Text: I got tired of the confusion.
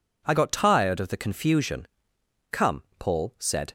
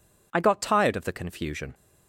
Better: second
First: goes on to say "Come Paul said"; noticeable; from 2.5 s on; 1.2 s long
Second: none

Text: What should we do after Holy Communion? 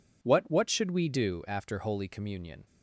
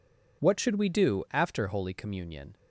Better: second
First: says "What" twice; at 0.4 s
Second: none

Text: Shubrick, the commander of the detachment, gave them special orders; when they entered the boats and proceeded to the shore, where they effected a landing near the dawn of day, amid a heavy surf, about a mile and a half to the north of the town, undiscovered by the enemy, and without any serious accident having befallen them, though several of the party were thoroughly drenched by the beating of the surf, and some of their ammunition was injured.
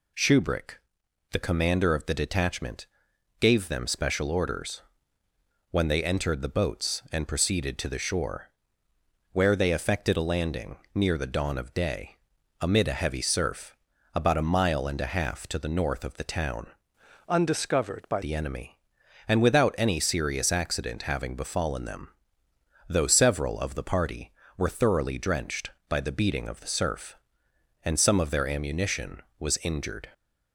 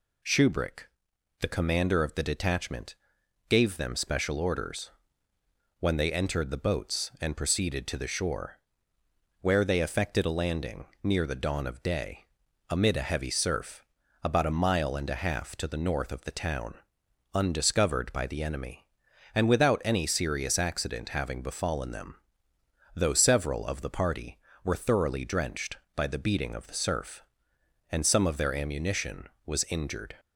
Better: second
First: pauses between "landing" and "near"; slight; at 10.7 s; 0.16 s long // changes voice from "undiscovered" to "by"; from 17.2 to 18.2 s; 1.0 s long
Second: pauses between "landing" and "near"; slight; at 10.8 s; 0.16 s long

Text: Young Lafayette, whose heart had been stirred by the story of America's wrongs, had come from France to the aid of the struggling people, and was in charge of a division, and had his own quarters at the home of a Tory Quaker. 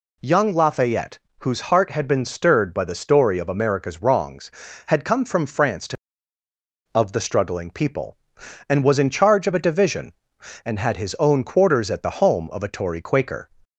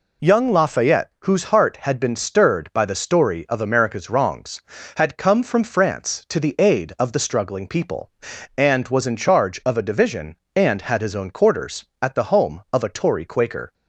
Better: second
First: skips "the aid"; at 6.4 s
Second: none

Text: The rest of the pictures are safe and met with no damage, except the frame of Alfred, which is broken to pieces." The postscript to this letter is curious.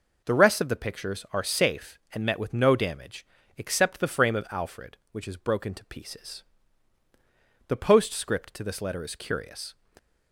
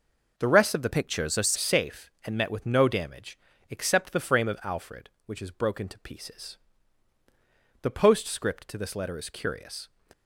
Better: first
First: none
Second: changes voice from "pictures" to "are"; from 0.9 to 1.5 s; 0.6 s long

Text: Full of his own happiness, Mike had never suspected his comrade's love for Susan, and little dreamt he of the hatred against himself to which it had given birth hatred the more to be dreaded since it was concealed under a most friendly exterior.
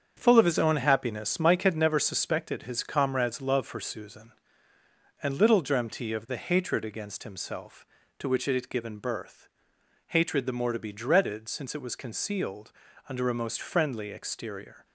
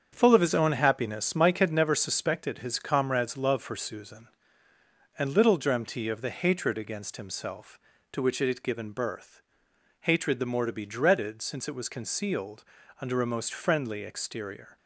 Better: neither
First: starts louder than the rest; strong; until 1.1 s; 7.5 dB // pauses between "birth" and "hatred"; noticeable; at 9.4 s; 0.60 s long // pauses between "concealed" and "under"; at 12.7 s; 0.38 s long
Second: starts louder than the rest; strong; until 1.1 s; 7.5 dB // pauses between "birth" and "hatred"; noticeable; at 9.4 s; 0.60 s long // pauses between "concealed" and "under"; at 12.6 s; 0.38 s long

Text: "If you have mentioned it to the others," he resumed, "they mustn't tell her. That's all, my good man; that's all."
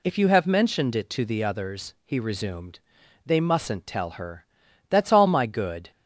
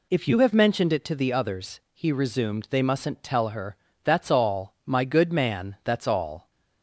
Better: second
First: stops before "man that's all"; at 5.9 s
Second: none

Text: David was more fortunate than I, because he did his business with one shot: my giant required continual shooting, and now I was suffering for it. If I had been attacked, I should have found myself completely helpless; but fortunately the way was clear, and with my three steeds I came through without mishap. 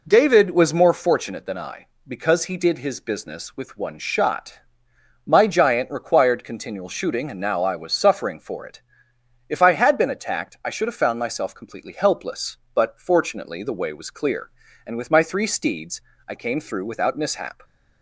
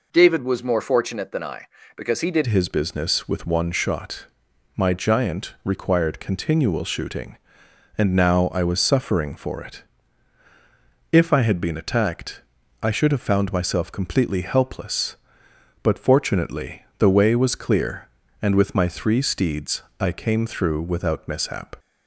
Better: first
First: pauses between "steeds" and "I"; slight; at 16.0 s; 0.26 s long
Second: changes voice at "his"; from 2.4 s on; 19.3 s long // pauses between "fortunately" and "the"; slight; at 16.8 s; 0.16 s long // pauses between "steeds" and "I"; slight; at 19.8 s; 0.18 s long

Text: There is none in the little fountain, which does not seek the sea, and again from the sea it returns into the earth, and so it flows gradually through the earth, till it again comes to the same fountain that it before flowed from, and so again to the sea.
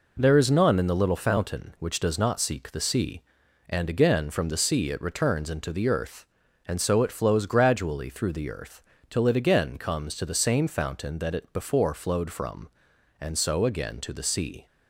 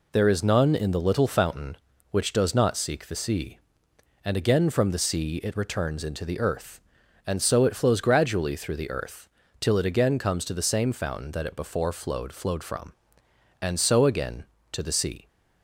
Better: first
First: none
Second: says "flowed" twice; at 12.3 s

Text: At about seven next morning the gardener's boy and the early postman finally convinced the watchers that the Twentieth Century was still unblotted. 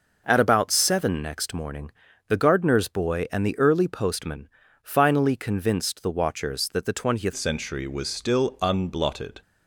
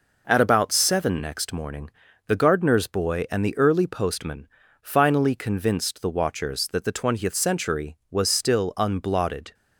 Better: second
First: pauses between "morning" and "the"; at 1.9 s; 0.38 s long // pauses between "postman" and "finally"; slight; at 4.4 s; 0.34 s long // changes voice at "Century"; from 7.3 s on; 2.1 s long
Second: pauses between "morning" and "the"; at 1.8 s; 0.38 s long // pauses between "postman" and "finally"; slight; at 4.4 s; 0.34 s long

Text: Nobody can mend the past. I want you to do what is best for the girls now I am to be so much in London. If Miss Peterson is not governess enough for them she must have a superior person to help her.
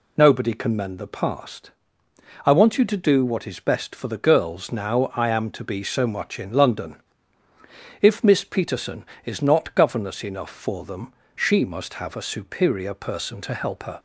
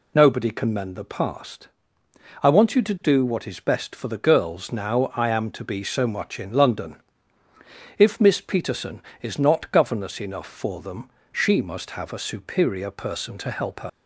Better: first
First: pauses between "them" and "she"; slight; at 11.1 s; 0.24 s long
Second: pauses between "them" and "she"; slight; at 11.0 s; 0.24 s long // leaves "her" unfinished; at 13.8 s; 60 ms

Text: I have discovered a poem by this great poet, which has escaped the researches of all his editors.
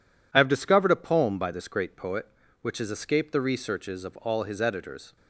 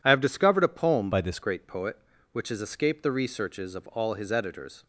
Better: first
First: none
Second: changes voice from "by" to "this"; from 1.1 to 1.3 s; 0.2 s long

